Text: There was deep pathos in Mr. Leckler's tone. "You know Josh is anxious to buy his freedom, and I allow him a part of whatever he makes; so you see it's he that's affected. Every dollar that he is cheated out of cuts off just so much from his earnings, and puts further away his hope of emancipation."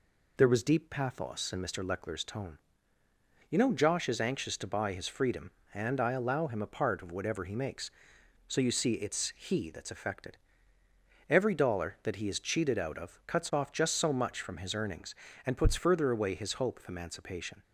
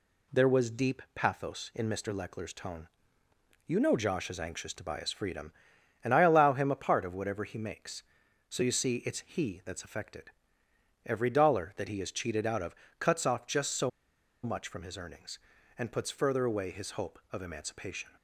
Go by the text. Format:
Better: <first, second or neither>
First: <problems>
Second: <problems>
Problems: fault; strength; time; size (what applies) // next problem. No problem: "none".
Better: first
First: none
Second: pauses between "of" and "cuts"; slight; at 12.7 s; 0.24 s long // pauses between "so" and "much"; noticeable; at 13.8 s; 0.53 s long